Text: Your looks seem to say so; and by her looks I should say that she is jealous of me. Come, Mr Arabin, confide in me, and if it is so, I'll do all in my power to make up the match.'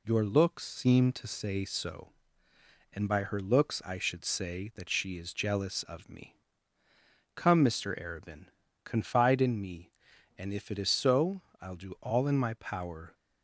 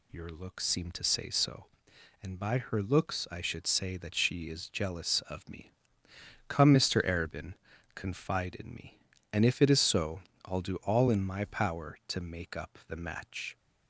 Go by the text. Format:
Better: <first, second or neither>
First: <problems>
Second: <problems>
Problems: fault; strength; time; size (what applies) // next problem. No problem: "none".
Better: second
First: stops before "to make up the match"; at 13.1 s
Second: none